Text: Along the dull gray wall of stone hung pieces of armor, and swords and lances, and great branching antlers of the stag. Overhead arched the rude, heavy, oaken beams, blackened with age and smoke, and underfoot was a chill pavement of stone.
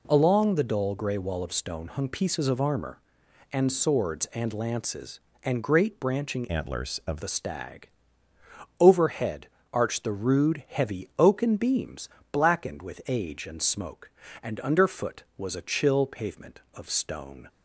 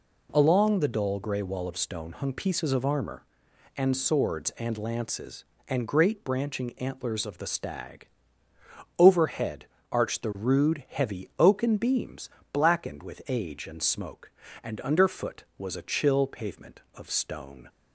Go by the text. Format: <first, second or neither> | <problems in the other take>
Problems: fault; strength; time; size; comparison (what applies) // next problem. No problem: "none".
second | changes voice from "antlers" to "of"; from 6.4 to 7.2 s; 0.8 s long // pauses between "Overhead" and "arched"; slight; at 9.4 s; 0.24 s long; slight in the second